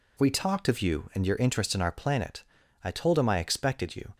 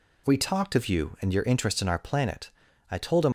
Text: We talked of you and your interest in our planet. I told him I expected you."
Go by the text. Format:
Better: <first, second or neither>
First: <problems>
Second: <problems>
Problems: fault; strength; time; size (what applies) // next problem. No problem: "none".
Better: first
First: none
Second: stops before "I expected you"; at 3.2 s